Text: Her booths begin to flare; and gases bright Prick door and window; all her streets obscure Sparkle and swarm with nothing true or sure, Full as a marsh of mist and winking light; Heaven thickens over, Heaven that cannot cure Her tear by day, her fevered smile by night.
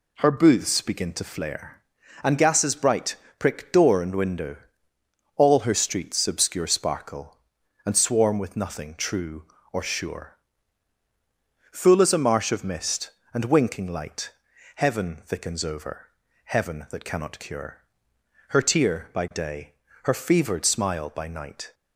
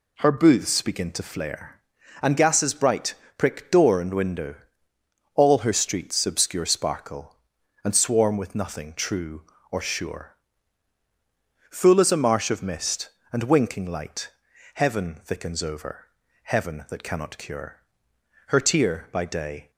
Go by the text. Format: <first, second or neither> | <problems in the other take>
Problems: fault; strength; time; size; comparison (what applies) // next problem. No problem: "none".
first | pauses between "bright" and "Prick"; slight; at 3.1 s; 0.24 s long; slight in the first // pauses between "cure" and "Her"; noticeable; at 17.8 s; 0.66 s long; noticeable in the first // stops before "her fevered smile by night"; at 19.7 s